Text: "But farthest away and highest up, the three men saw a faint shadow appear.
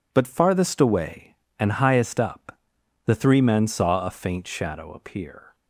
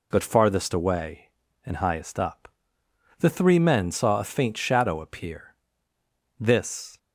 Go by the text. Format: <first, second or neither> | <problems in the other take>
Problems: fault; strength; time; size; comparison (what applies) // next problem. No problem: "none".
first | goes on to say "This"; from 6.3 s on; 0.60 s long